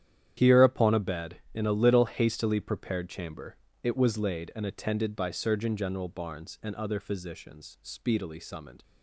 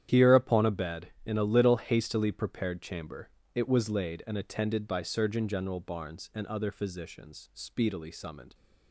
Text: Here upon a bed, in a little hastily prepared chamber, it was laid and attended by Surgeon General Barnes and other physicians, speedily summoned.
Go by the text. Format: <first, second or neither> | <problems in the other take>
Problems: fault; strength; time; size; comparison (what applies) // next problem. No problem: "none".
neither | starts louder than the rest; strong; the same in both